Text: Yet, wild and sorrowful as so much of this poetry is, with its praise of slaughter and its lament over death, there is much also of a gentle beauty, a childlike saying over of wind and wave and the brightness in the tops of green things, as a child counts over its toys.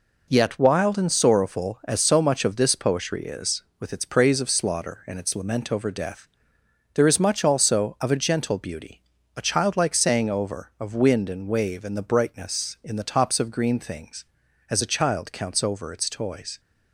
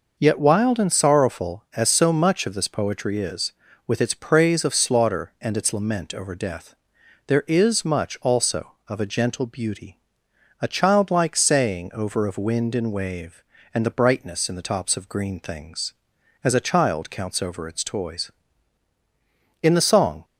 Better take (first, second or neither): first